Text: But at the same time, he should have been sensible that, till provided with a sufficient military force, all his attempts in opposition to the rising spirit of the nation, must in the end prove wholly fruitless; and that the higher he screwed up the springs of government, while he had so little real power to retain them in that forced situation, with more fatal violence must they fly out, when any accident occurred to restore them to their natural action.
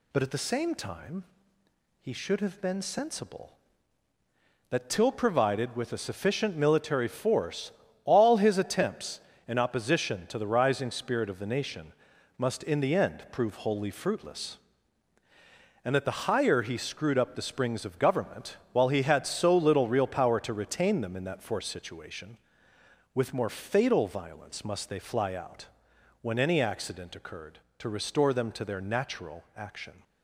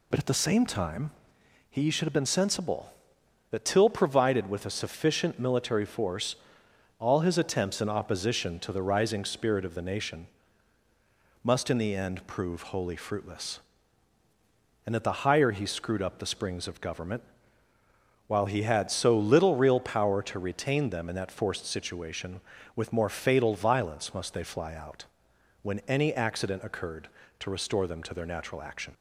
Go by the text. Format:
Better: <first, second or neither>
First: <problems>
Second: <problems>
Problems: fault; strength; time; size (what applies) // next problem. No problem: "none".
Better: neither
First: none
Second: none